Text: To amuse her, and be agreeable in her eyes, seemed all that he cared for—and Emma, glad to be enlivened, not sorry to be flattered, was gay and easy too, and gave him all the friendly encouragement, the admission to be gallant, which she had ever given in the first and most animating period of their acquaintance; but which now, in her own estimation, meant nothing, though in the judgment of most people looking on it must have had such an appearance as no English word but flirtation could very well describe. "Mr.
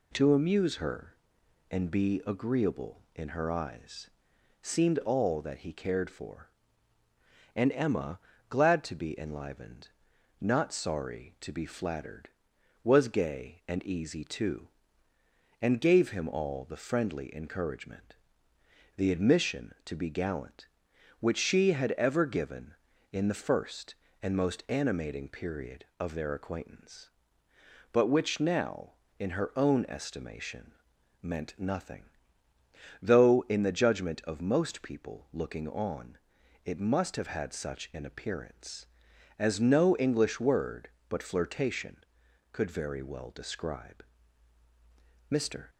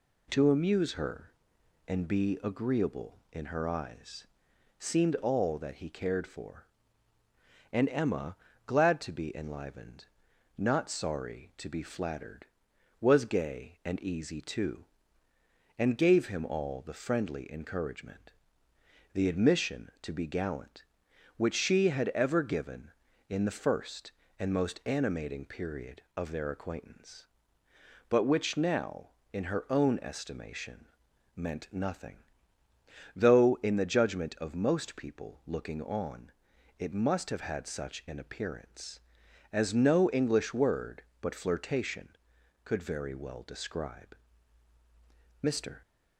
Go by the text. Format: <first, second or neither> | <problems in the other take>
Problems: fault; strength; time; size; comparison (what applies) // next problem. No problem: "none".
neither | pauses between "on" and "it"; noticeable; the same in both